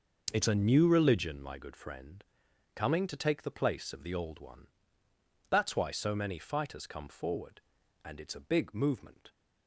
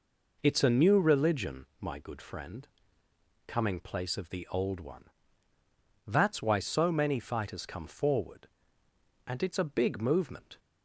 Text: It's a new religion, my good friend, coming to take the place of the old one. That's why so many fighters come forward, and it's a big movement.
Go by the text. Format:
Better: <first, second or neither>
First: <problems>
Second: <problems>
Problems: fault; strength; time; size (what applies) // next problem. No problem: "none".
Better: first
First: none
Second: skips "to take the"; at 3.8 s